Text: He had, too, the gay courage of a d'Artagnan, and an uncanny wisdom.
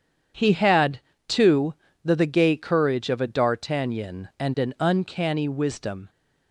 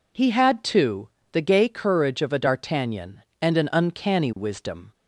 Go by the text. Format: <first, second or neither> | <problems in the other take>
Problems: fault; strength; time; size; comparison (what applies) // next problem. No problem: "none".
second | says "the" twice; at 2.1 s